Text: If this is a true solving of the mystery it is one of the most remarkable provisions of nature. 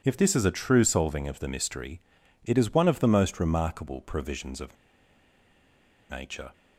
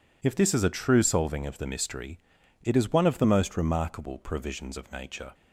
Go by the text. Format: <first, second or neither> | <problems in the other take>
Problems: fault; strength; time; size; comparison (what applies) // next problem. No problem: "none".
second | pauses between "mystery" and "it"; at 2.0 s; 0.44 s long; also in the second // pauses between "of" and "nature"; strong; at 4.7 s; 1.3 s long